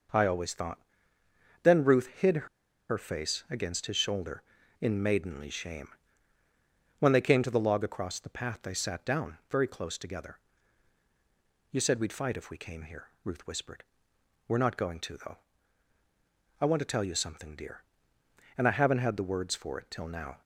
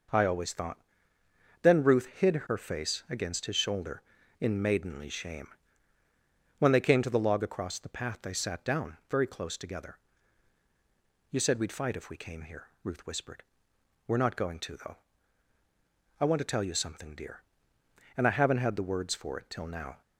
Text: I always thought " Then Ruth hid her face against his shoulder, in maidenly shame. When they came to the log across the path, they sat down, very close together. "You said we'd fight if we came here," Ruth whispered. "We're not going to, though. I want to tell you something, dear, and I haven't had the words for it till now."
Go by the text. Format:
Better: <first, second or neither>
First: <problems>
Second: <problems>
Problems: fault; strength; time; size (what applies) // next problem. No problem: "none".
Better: second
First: pauses between "hid" and "her"; at 2.4 s; 0.41 s long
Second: none